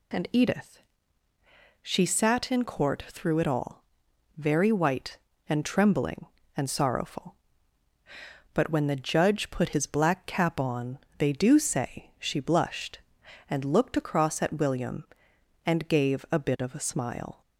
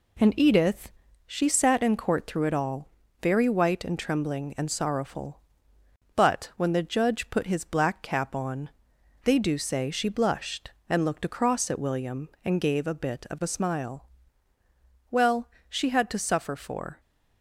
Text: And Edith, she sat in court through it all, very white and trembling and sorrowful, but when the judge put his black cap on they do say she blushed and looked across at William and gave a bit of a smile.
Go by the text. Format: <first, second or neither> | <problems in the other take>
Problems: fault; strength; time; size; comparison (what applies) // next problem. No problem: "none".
first | pauses between "on" and "they"; noticeable; at 8.6 s; 0.54 s long; slight in the first // goes on to say "Well she had to suffer for"; strong; from 15.1 s on; 1.8 s long